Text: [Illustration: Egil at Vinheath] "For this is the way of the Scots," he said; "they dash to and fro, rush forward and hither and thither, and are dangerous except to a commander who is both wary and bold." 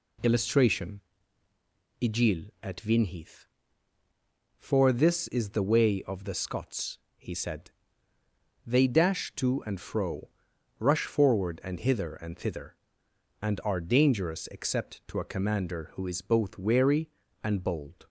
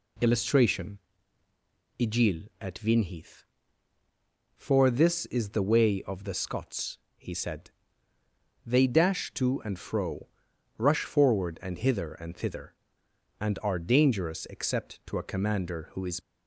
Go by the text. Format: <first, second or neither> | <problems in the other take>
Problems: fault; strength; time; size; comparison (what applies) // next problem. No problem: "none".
first | stops before "both wary and bold"; at 16.2 s